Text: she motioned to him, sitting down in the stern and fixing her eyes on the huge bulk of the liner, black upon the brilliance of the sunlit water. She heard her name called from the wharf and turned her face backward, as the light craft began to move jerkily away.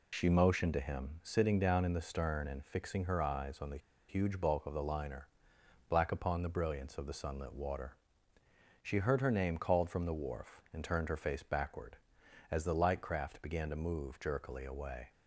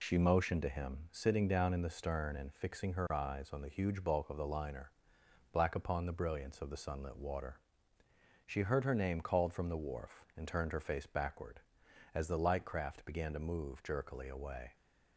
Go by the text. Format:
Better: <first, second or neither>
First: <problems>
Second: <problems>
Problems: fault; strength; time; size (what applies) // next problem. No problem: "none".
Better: second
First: pauses between "the" and "huge"; slight; at 3.7 s; 0.30 s long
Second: none